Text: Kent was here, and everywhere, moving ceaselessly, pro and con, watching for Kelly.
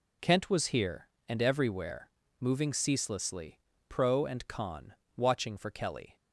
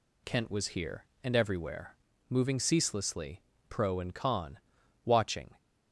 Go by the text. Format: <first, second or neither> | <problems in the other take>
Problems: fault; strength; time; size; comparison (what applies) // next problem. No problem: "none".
first | stops before "for Kelly"; at 5.5 s